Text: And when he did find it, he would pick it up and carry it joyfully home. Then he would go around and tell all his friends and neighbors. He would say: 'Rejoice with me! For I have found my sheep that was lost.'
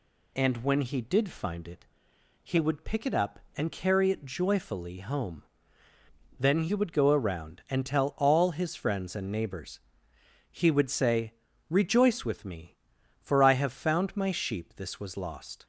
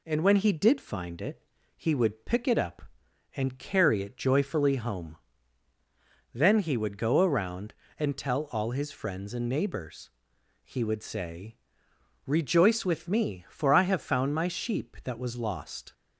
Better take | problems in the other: second | says "this" for "that"; at 14.7 s

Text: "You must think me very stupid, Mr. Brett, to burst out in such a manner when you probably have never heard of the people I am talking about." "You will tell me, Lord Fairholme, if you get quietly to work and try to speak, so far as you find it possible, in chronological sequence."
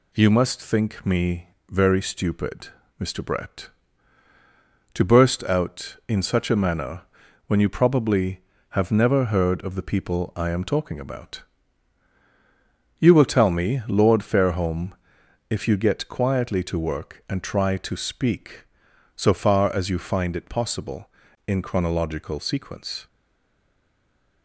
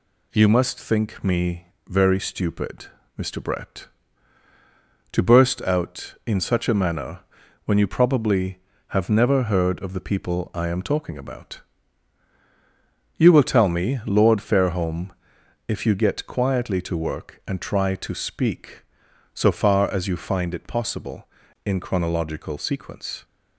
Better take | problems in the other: second | pauses between "me" and "very"; slight; at 1.4 s; 0.22 s long; slight in the second // pauses between "manner" and "when"; noticeable; at 7.0 s; 0.46 s long; noticeable in the second // stays silent after the last word; noticeable; from 23.0 s on; 1.4 s long

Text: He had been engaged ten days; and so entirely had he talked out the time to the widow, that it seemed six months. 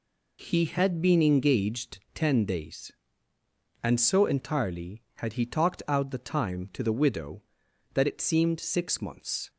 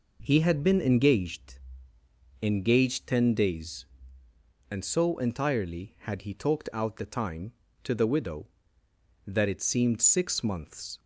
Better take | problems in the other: first | says "engaged" twice; at 2.4 s

